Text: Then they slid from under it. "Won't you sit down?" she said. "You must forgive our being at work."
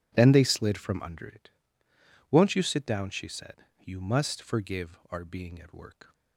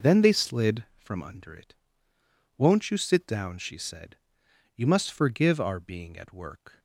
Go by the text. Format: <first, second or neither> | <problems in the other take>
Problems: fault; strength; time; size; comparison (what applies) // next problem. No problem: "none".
neither | none